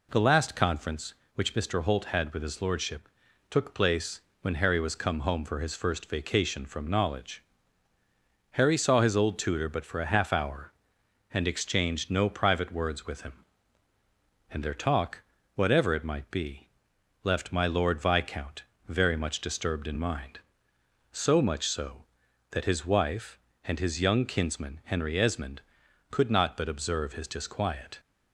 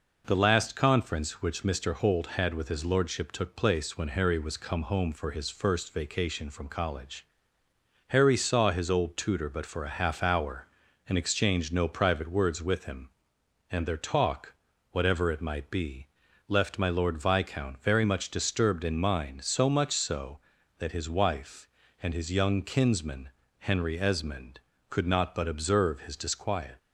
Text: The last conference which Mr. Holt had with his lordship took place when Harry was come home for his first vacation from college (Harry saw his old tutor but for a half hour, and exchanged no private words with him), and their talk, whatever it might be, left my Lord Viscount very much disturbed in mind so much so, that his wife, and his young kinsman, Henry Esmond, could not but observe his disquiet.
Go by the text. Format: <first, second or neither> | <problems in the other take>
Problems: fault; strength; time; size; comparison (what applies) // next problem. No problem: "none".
second | pauses between "lordship" and "took"; at 3.0 s; 0.40 s long // pauses between "place" and "when"; slight; at 4.2 s; 0.20 s long // says "knowledge" for "college"; at 6.8 s // pauses between "Viscount" and "very"; slight; at 18.6 s; 0.24 s long